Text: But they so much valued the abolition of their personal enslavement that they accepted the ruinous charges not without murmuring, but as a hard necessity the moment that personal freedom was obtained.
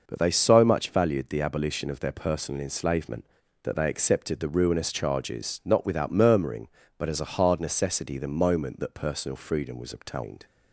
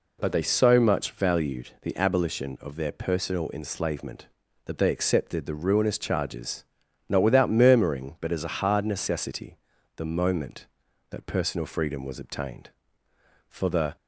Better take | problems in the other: first | pauses between "charges" and "not"; noticeable; at 6.6 s; 0.48 s long // pauses between "necessity" and "the"; at 9.5 s; 0.38 s long // goes on to say "For the"; slight; from 13.4 s on; 0.46 s long

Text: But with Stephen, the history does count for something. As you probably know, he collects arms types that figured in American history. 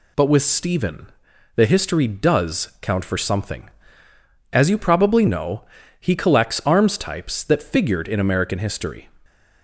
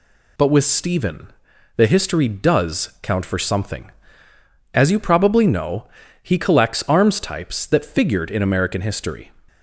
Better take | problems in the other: neither | none

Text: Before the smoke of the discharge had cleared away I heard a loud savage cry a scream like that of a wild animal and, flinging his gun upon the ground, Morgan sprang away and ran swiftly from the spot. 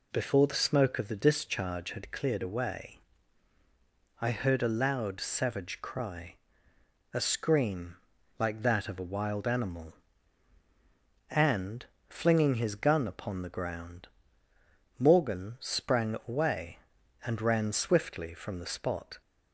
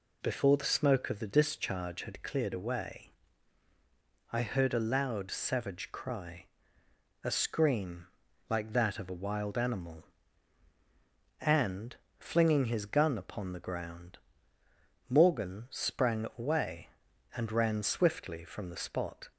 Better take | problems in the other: neither | pauses between "away" and "I"; the same in both // pauses between "cry" and "a"; noticeable; the same in both // pauses between "scream" and "like"; the same in both

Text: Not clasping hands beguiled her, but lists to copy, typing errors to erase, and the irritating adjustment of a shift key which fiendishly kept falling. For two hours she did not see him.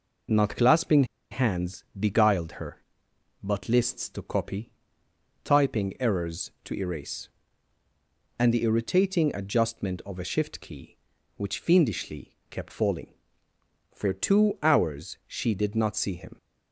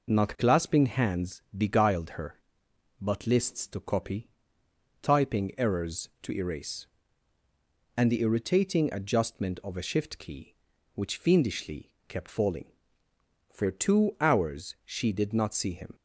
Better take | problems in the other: second | pauses between "clasping" and "hands"; slight; at 1.0 s; 0.25 s long // pauses between "hands" and "beguiled"; slight; at 1.8 s; 0.16 s long; slight in the second // pauses between "fiendishly" and "kept"; slight; at 12.3 s; 0.16 s long; slight in the second

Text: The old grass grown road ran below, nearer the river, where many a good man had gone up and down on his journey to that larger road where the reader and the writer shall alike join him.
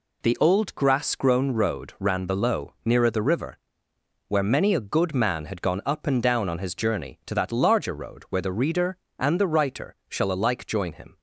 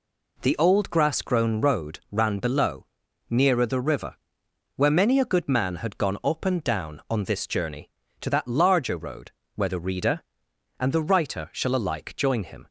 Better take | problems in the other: first | says "this" for "his"; at 7.2 s // pauses between "road" and "where"; slight; at 9.3 s; 0.24 s long

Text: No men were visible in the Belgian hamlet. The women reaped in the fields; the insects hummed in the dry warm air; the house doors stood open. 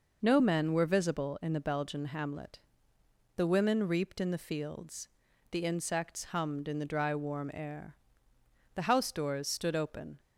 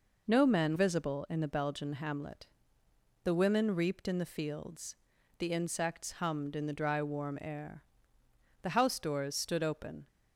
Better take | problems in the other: first | skips "were"; at 0.7 s

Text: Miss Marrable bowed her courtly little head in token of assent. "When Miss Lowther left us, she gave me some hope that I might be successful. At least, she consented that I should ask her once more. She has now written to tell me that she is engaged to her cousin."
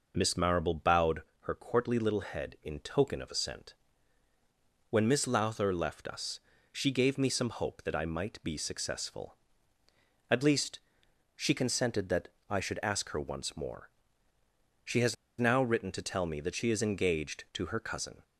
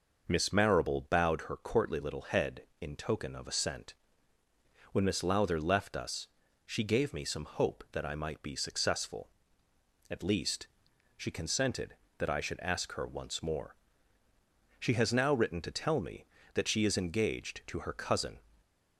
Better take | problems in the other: second | pauses between "bowed" and "her"; slight; at 1.2 s; 0.18 s long // pauses between "that" and "I"; slight; at 12.2 s; 0.18 s long // pauses between "has" and "now"; slight; at 15.1 s; 0.25 s long

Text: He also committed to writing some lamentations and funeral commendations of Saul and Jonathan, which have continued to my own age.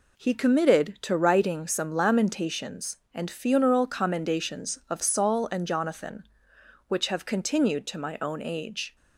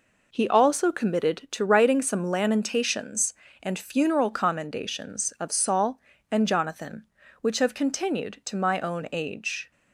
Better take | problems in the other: second | skips "also"; at 0.3 s

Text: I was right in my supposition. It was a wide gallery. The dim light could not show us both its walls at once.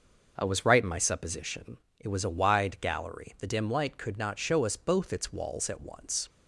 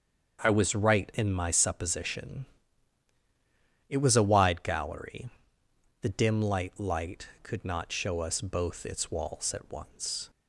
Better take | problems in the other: first | starts louder than the rest; strong; until 1.4 s; 7 dB; noticeable in the first // says "light" twice; at 6.7 s

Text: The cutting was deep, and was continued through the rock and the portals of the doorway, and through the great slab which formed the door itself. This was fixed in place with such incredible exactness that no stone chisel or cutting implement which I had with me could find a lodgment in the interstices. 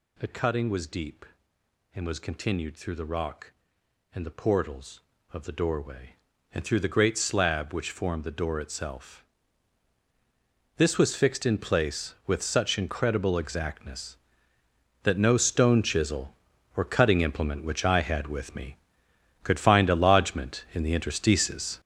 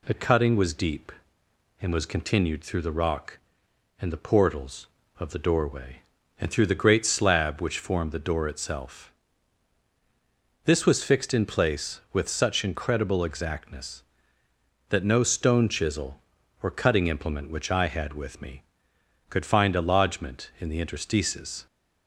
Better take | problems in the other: second | gets louder; strong; throughout; 9.5 dB

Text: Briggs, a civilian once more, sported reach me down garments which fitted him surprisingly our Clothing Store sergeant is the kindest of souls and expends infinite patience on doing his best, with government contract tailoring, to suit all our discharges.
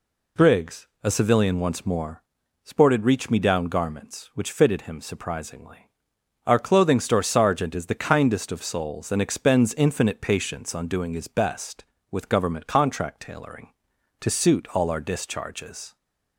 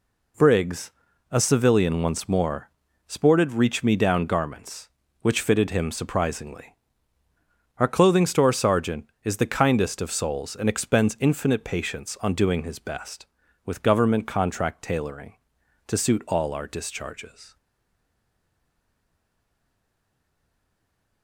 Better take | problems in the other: first | pauses between "surprisingly" and "our"; at 6.7 s; 1.0 s long; noticeable in the first // stays silent after the last word; strong; from 17.5 s on; 3.7 s long

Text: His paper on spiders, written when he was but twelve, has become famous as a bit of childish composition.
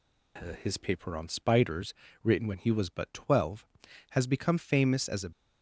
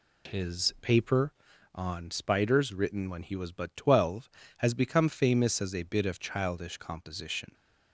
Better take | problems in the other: second | stops before "bit of childish composition"; at 5.3 s

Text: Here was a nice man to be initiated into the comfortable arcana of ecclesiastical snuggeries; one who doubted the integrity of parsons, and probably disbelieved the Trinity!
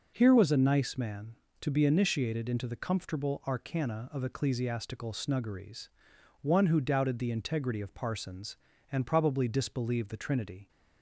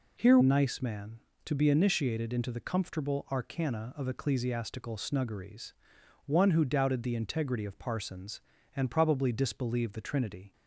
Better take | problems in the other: first | skips "was a"; at 0.4 s

